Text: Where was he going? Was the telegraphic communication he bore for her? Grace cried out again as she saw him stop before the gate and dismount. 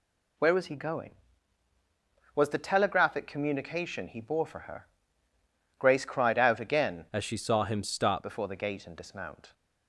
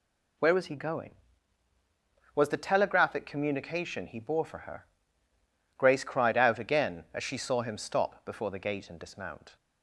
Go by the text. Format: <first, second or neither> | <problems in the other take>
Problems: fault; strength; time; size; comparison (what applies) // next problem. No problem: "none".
second | changes voice from "as" to "stop"; from 7.1 to 8.2 s; 1.1 s long